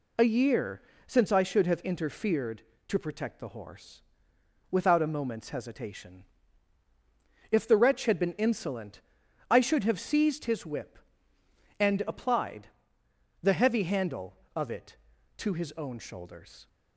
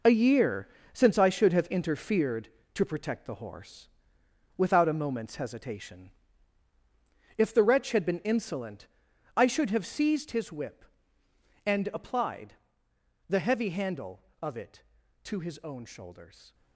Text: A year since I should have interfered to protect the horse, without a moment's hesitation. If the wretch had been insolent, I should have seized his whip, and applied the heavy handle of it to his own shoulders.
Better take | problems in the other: first | gets quieter; strong; throughout; 9.5 dB // pauses between "year" and "since"; slight; at 0.6 s; 0.24 s long; slight in the first // pauses between "applied" and "the"; noticeable; at 12.5 s; 0.74 s long; noticeable in the first

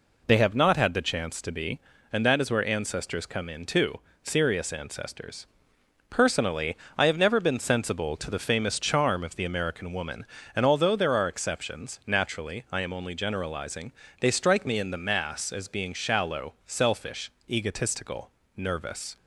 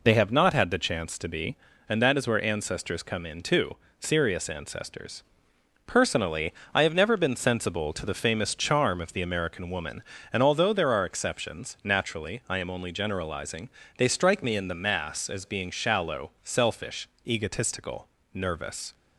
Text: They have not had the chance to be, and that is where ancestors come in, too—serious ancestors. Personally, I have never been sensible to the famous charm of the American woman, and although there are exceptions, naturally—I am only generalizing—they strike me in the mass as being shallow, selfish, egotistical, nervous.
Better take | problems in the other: neither | none

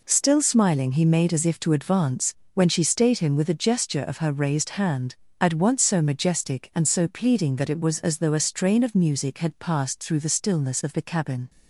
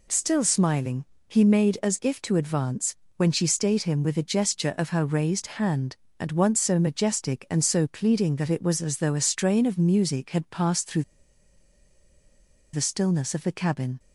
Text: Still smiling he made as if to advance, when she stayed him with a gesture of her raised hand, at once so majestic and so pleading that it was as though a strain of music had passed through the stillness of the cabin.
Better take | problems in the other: first | pauses between "smiling" and "he"; slight; at 1.0 s; 0.24 s long // pauses between "through" and "the"; strong; at 11.0 s; 1.7 s long

